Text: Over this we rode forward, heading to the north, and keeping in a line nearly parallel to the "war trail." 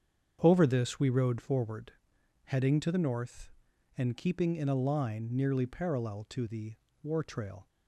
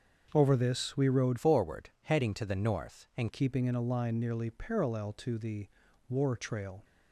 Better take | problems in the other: first | starts louder than the rest; until 1.3 s; 6.5 dB; strong in the first // changes voice from "forward" to "and"; from 1.3 to 3.3 s; 2.0 s long // pauses between "the" and "war"; at 5.6 s; 0.40 s long; slight in the first

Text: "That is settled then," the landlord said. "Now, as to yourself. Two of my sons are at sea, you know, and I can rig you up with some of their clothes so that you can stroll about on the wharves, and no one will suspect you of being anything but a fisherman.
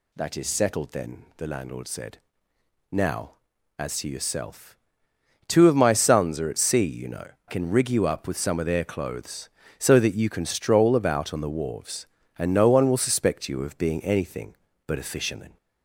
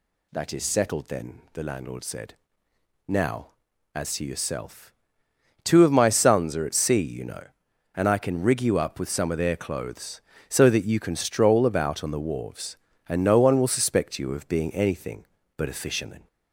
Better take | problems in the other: second | skips "and I"; at 7.3 s

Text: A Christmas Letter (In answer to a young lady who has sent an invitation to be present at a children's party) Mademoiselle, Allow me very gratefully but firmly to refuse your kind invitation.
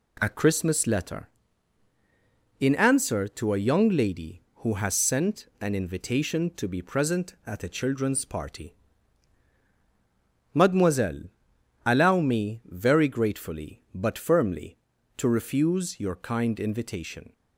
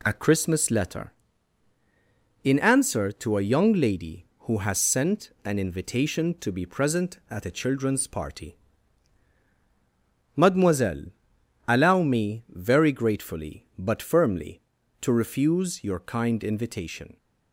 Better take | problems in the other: neither | none

